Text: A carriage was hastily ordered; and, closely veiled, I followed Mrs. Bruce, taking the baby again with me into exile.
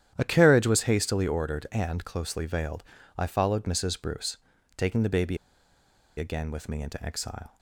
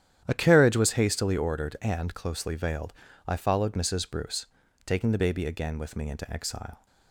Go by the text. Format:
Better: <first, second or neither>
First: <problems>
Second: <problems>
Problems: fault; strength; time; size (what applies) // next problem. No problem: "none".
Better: second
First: starts louder than the rest; strong; until 1.1 s; 10.5 dB // pauses between "baby" and "again"; noticeable; at 5.3 s; 0.80 s long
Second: starts louder than the rest; strong; until 1.2 s; 10.5 dB